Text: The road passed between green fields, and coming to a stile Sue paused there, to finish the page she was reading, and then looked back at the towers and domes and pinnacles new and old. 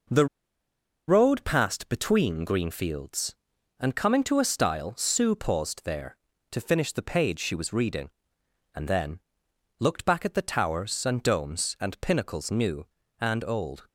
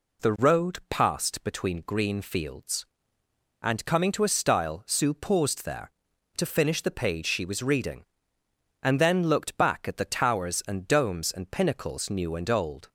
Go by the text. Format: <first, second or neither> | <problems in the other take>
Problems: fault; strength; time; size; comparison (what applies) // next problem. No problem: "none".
second | pauses between "The" and "road"; noticeable; at 0.2 s; 0.82 s long // pauses between "then" and "looked"; noticeable; at 9.1 s; 0.60 s long